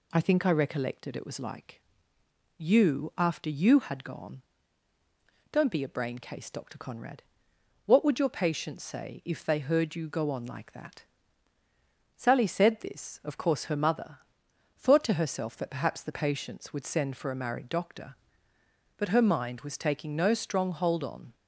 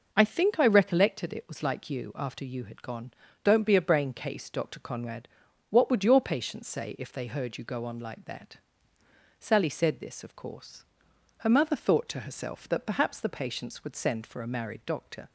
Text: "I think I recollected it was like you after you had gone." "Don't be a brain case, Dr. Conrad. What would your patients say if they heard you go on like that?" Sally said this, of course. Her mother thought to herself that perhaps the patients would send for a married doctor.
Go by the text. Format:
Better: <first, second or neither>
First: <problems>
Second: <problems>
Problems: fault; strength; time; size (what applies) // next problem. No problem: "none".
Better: second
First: pauses between "like" and "you"; noticeable; at 1.8 s; 0.76 s long // pauses between "mother" and "thought"; noticeable; at 14.2 s; 0.58 s long // goes on to say "But her mind was taking no strong hold on"; strong; from 18.9 s on; 2.3 s long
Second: none